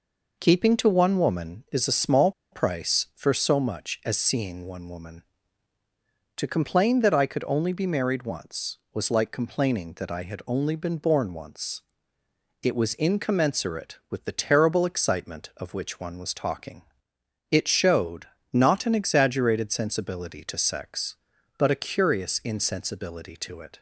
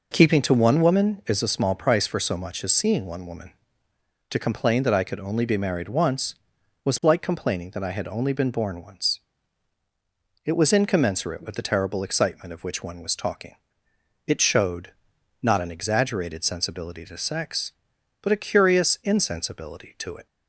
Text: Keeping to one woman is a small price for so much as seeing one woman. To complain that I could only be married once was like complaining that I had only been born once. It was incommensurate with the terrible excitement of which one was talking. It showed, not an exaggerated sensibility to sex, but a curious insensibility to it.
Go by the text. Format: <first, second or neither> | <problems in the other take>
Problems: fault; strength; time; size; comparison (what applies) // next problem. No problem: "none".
second | pauses between "small" and "price"; slight; at 2.3 s; 0.21 s long